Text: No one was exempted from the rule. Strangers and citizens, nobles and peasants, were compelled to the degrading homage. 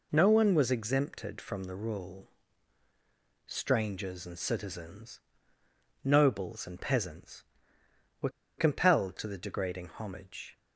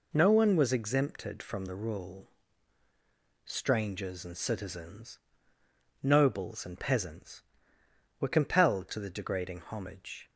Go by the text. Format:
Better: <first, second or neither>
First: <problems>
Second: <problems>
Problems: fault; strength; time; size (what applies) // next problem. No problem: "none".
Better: second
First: pauses between "were" and "compelled"; slight; at 8.2 s; 0.29 s long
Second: none